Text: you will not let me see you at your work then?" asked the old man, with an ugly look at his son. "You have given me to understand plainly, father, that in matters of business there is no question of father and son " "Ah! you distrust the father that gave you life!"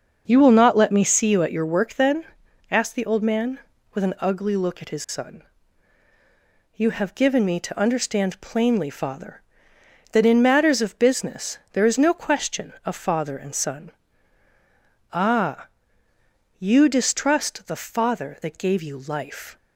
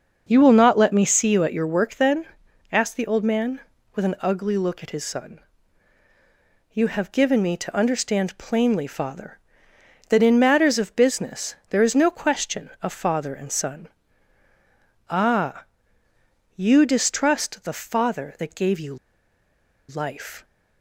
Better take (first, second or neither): first